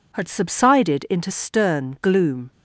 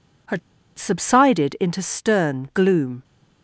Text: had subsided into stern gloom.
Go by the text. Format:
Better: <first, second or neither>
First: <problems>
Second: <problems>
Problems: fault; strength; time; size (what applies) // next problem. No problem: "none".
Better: first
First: none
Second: pauses between "had" and "subsided"; at 0.3 s; 0.39 s long